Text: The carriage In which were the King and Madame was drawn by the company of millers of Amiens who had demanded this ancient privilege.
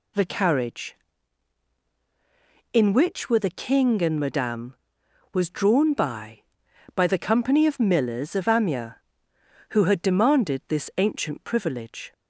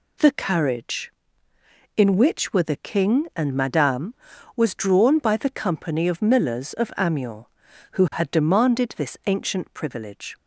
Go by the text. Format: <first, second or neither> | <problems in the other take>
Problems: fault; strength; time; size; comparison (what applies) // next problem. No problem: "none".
second | says "by" twice; at 6.9 s